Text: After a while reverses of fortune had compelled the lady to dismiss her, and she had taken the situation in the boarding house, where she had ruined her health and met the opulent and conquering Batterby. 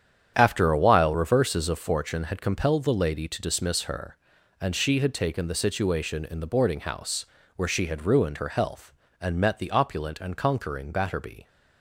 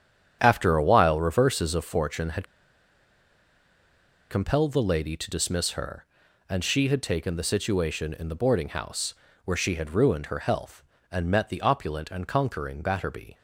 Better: first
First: starts louder than the rest; strong; until 1.3 s; 9 dB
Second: starts louder than the rest; strong; until 1.4 s; 9 dB // pauses between "had" and "compelled"; strong; at 2.4 s; 1.8 s long

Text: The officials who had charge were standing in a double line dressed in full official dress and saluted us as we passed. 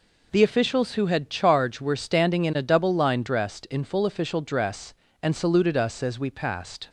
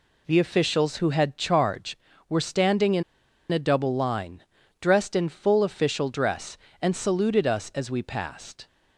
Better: first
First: none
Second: pauses between "in" and "a"; noticeable; at 3.0 s; 0.49 s long // pauses between "line" and "dressed"; at 4.4 s; 0.38 s long

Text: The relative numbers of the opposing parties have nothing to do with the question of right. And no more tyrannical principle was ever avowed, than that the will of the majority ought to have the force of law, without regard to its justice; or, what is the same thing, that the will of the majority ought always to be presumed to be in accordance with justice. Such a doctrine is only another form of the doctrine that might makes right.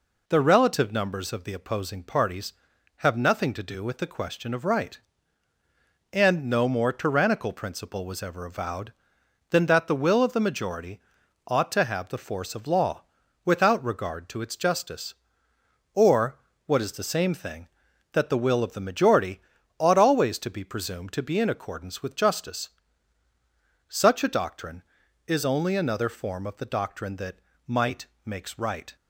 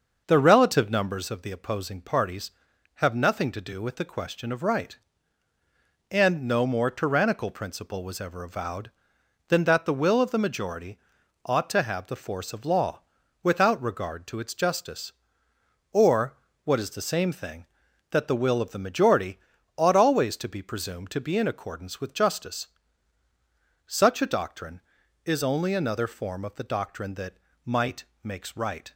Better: first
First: pauses between "majority" and "ought"; noticeable; at 10.9 s; 0.46 s long // pauses between "majority" and "ought"; at 19.3 s; 0.38 s long // pauses between "that" and "might"; slight; at 27.3 s; 0.30 s long // pauses between "might" and "makes"; slight; at 28.0 s; 0.18 s long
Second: starts louder than the rest; noticeable; until 1.3 s; 6 dB // pauses between "majority" and "ought"; noticeable; at 10.9 s; 0.46 s long // pauses between "majority" and "ought"; at 19.3 s; 0.38 s long // pauses between "that" and "might"; slight; at 27.3 s; 0.30 s long // pauses between "might" and "makes"; slight; at 28.0 s; 0.18 s long

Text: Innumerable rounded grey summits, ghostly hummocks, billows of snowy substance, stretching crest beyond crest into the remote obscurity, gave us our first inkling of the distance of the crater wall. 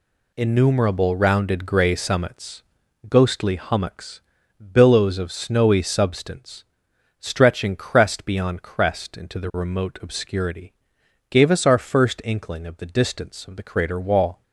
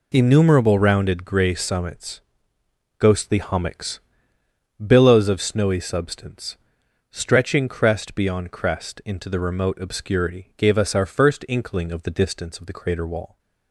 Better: neither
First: none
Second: none

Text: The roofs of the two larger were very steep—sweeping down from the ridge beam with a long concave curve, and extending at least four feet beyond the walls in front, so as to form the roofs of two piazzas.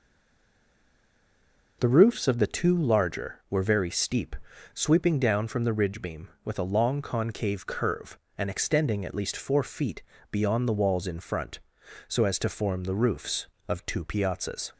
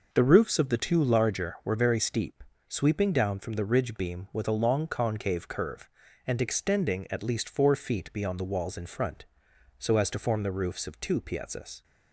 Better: second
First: stays silent before the first word; noticeable; until 1.8 s; 1.8 s long // pauses between "feet" and "beyond"; slight; at 10.0 s; 0.30 s long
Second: none

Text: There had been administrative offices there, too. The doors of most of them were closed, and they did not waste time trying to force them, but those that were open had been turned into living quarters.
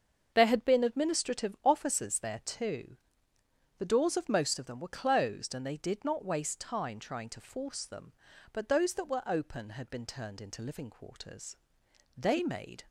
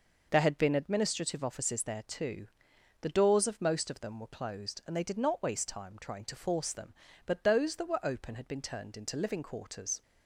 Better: second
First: starts louder than the rest; until 1.3 s; 6.5 dB // goes on to say "They made"; noticeable; from 12.1 s on; 0.68 s long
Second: none

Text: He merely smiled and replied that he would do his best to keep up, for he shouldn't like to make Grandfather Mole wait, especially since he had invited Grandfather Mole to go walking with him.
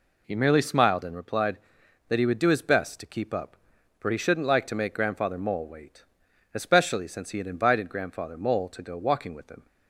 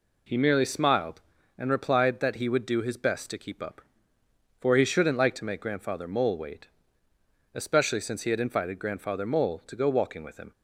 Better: neither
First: none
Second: none

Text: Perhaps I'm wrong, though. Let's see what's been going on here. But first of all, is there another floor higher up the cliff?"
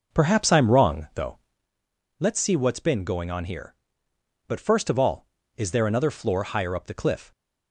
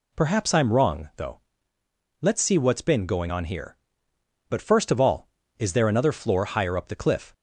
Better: second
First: starts louder than the rest; noticeable; until 1.6 s; 6 dB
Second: none

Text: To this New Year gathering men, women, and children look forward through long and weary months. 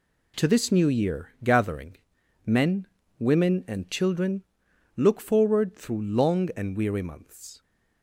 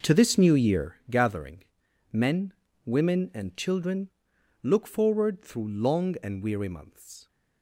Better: first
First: pauses between "Year" and "gathering"; slight; at 1.2 s; 0.16 s long // pauses between "gathering" and "men"; noticeable; at 1.9 s; 0.48 s long // pauses between "children" and "look"; noticeable; at 4.4 s; 0.54 s long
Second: starts louder than the rest; noticeable; until 0.9 s; 5.5 dB // pauses between "Year" and "gathering"; slight; at 0.9 s; 0.16 s long // pauses between "gathering" and "men"; noticeable; at 1.6 s; 0.48 s long // pauses between "children" and "look"; noticeable; at 4.0 s; 0.54 s long

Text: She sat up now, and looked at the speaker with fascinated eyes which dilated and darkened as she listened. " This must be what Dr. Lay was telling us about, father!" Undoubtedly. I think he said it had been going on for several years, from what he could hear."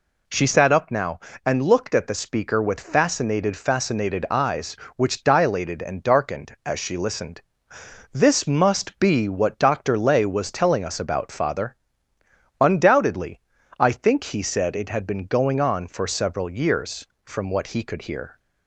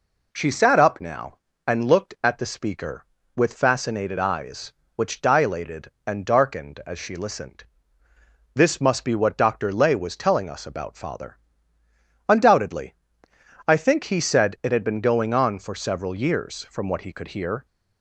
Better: second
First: says "fascinated" twice; at 3.5 s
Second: none

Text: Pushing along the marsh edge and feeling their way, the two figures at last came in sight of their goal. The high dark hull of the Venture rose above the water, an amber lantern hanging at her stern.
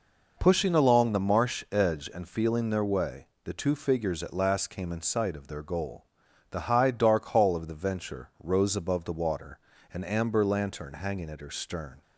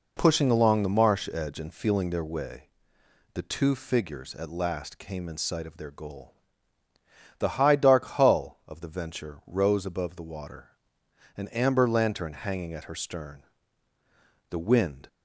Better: first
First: none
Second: goes on to say "The wind"; from 14.4 s on; 0.58 s long

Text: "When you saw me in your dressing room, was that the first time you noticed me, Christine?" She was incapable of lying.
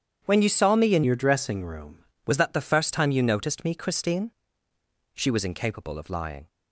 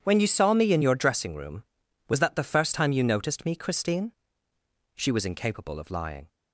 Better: second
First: starts louder than the rest; strong; until 1.2 s; 8.5 dB // changes voice from "your" to "room"; from 1.0 to 1.9 s; 0.9 s long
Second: none

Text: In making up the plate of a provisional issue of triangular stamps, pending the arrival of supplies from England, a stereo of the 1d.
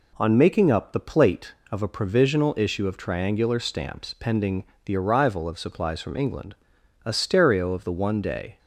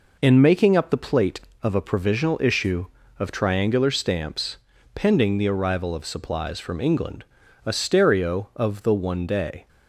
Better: second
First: says "On" for "In"; at 0.1 s // pauses between "pending" and "the"; slight; at 4.6 s; 0.22 s long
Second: none

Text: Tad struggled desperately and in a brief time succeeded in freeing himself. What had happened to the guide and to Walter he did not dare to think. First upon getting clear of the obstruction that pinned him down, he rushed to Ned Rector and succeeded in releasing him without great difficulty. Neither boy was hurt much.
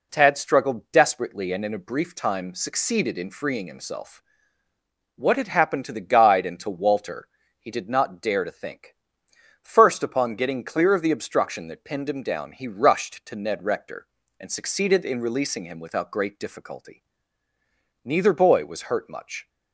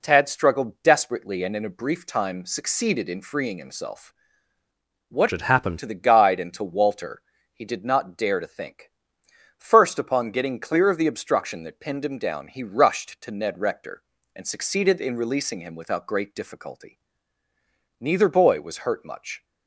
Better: first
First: pauses between "Walter" and "he"; slight; at 7.2 s; 0.32 s long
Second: changes voice from "had" to "happened"; from 5.3 to 5.7 s; 0.4 s long // pauses between "Walter" and "he"; slight; at 7.2 s; 0.32 s long

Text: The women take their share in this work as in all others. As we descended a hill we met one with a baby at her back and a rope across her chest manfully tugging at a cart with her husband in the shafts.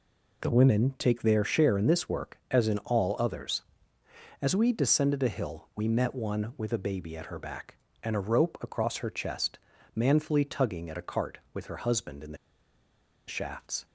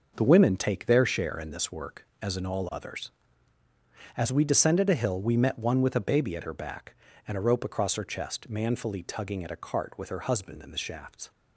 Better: second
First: pauses between "chest" and "manfully"; slight; at 9.5 s; 0.36 s long // pauses between "the" and "shafts"; noticeable; at 12.3 s; 0.92 s long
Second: none

